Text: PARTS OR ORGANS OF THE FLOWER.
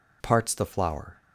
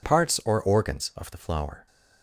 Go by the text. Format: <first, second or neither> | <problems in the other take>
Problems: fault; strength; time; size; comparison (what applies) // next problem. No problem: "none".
second | skips "OR ORGANS OF"; at 0.5 s